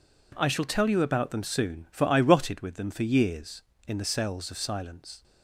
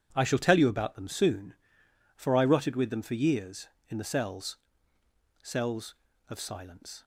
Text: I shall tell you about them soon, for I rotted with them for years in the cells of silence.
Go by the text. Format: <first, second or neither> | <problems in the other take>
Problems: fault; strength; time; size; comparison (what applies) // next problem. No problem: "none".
first | says "cells" twice; at 5.4 s